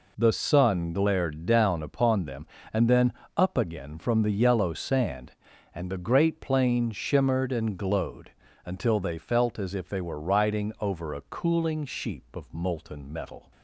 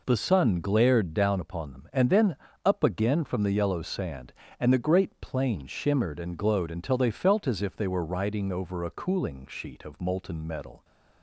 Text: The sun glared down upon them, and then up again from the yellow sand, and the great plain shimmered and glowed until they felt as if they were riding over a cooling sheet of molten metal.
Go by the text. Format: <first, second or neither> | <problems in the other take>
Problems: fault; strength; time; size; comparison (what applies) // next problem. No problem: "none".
second | pauses between "then" and "up"; slight; at 3.1 s; 0.24 s long; slight in the second // pauses between "glowed" and "until"; slight; at 8.3 s; 0.32 s long // says "sheep" for "sheet"; at 11.8 s